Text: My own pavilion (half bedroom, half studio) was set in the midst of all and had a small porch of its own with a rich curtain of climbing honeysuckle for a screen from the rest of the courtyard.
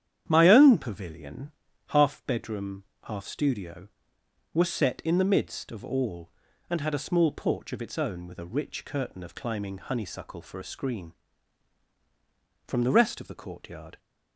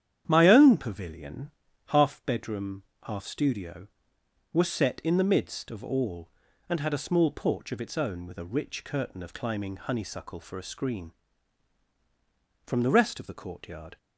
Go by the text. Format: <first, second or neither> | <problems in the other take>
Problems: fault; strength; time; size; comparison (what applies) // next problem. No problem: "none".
neither | starts louder than the rest; strong; the same in both